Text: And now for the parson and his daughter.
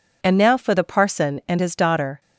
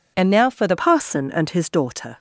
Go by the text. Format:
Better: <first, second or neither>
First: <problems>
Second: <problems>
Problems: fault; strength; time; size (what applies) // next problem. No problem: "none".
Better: first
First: none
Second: changes voice at "parson"; from 0.7 s on; 1.4 s long